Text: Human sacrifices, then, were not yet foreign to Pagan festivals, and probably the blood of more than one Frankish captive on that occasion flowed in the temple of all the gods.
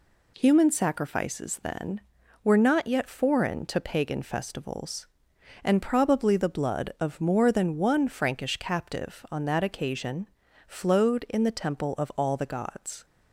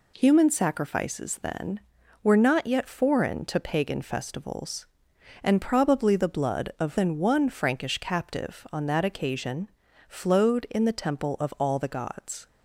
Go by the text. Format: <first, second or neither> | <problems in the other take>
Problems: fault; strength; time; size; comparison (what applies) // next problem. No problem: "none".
first | skips "more"; at 6.9 s // pauses between "occasion" and "flowed"; at 9.6 s; 0.38 s long; also in the first